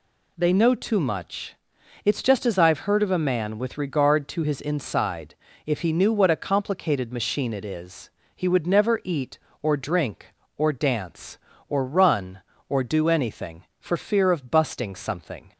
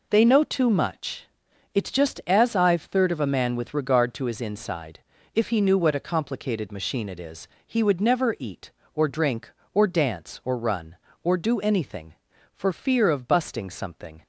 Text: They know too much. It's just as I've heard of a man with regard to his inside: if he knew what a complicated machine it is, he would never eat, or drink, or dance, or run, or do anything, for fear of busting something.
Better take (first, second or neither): first